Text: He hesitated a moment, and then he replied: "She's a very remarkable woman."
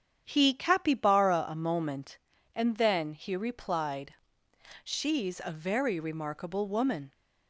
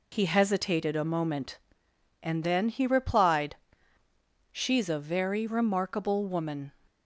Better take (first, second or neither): second